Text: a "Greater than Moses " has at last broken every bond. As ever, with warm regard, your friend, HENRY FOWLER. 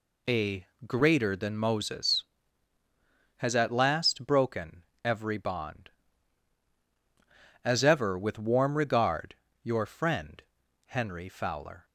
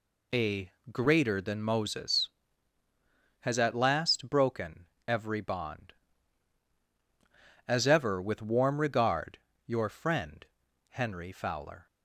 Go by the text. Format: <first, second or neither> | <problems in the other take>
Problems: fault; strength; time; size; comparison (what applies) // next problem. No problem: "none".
neither | pauses between "a" and "Greater"; slight; the same in both // pauses between "broken" and "every"; slight; the same in both